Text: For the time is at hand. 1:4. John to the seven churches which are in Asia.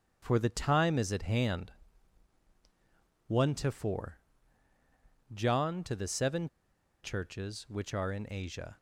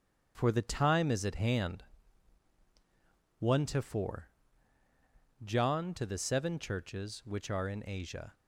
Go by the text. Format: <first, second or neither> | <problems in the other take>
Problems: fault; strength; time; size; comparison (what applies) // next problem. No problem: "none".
second | starts louder than the rest; strong; until 1.2 s; 7 dB; strong in the second // pauses between "seven" and "churches"; noticeable; at 6.4 s; 0.56 s long